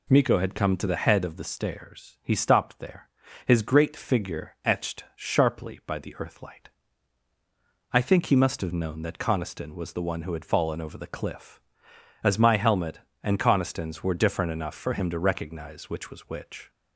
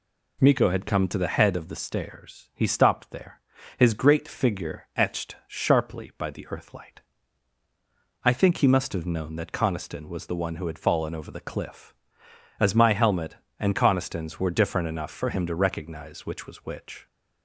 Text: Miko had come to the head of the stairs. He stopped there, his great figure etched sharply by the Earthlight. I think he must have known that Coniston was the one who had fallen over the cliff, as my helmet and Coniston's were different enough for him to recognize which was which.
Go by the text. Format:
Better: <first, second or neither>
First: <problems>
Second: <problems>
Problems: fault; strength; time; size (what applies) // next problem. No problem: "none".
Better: neither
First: none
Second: none